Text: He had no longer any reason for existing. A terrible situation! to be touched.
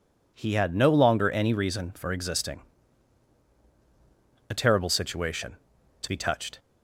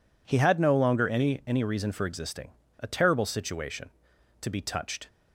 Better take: first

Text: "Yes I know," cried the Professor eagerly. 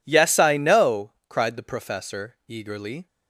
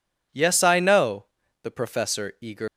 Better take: first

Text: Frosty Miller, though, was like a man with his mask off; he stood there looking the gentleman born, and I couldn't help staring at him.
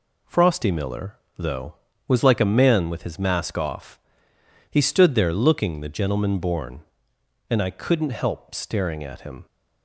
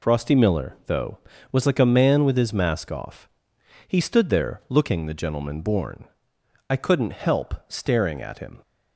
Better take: first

